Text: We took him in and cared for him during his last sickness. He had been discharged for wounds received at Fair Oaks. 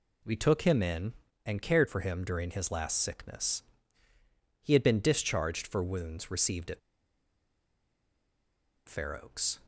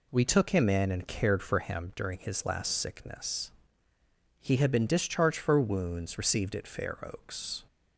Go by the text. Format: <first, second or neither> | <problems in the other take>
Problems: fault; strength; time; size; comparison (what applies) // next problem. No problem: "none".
second | pauses between "at" and "Fair"; strong; at 6.7 s; 2.0 s long